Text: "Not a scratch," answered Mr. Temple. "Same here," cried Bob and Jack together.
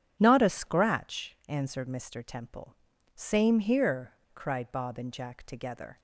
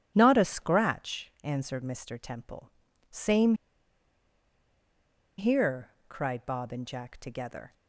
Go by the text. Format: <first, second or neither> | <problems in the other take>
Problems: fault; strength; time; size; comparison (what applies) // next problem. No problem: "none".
first | starts louder than the rest; strong; until 1.1 s; 9.5 dB; strong in the first // pauses between "Same" and "here"; strong; at 3.5 s; 1.8 s long